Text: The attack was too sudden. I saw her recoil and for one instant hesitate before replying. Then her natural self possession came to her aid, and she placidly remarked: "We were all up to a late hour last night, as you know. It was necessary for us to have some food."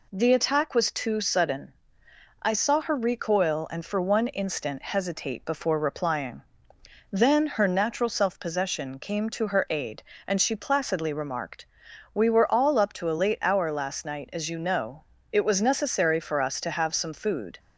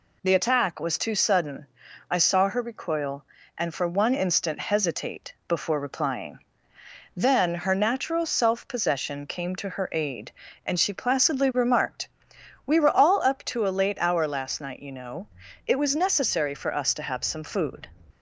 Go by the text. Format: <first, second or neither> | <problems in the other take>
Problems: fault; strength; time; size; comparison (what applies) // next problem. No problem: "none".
first | pauses between "hesitate" and "before"; slight; at 5.3 s; 0.16 s long // skips "as"; at 14.7 s